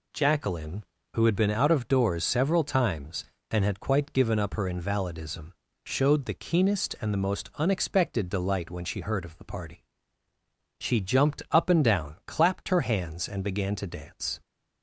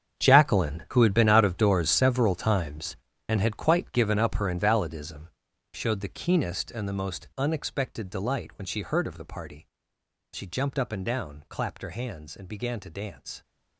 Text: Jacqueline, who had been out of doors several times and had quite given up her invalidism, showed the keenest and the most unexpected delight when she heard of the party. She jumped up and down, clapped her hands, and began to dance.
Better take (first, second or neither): first